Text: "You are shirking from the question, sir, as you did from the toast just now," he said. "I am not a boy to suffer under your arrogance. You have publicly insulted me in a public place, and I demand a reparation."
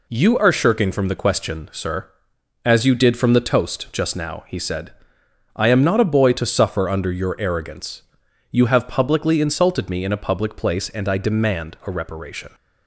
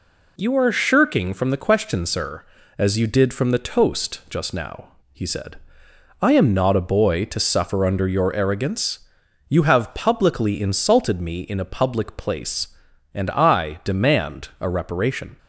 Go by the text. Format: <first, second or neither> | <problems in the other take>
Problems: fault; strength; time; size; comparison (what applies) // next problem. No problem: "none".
neither | none